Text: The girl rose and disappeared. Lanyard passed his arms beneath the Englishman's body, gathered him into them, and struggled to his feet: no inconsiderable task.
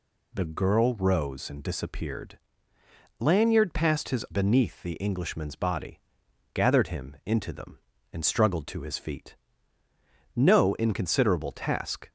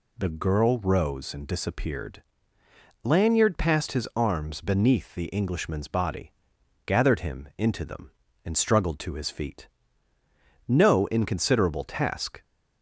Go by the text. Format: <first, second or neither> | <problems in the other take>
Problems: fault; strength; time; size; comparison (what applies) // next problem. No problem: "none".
second | skips "arms"; at 4.2 s